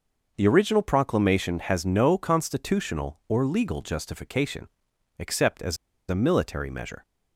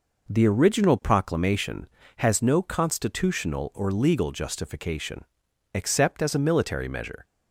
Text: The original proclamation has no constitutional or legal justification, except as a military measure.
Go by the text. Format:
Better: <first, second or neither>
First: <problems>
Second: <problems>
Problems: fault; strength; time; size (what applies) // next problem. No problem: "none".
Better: second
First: pauses between "as" and "a"; slight; at 5.7 s; 0.32 s long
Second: none